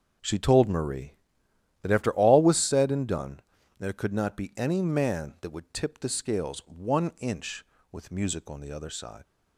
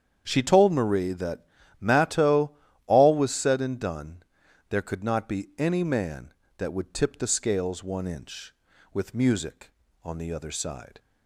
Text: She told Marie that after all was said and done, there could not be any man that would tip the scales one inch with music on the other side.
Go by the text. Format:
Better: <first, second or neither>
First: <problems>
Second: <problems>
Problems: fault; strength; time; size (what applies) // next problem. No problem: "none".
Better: first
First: starts louder than the rest; until 1.9 s; 6.5 dB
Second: starts louder than the rest; strong; until 1.2 s; 8.5 dB // says "matto" for "after"; at 1.8 s